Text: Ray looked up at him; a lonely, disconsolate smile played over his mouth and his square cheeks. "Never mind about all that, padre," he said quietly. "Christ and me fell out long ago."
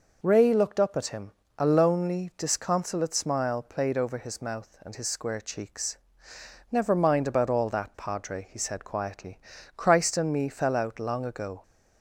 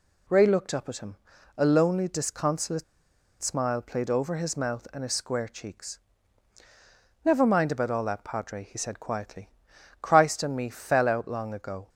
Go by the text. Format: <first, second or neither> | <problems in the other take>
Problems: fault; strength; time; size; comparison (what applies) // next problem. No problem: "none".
first | pauses between "disconsolate" and "smile"; noticeable; at 2.8 s; 0.58 s long